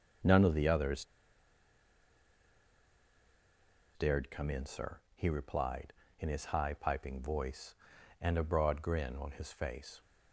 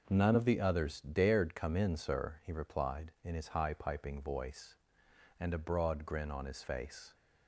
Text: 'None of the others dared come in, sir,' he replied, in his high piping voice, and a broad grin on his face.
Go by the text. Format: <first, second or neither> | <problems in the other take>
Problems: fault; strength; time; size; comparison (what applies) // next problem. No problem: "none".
second | starts louder than the rest; until 4.1 s; 6 dB // pauses between "others" and "dared"; strong; at 1.0 s; 2.8 s long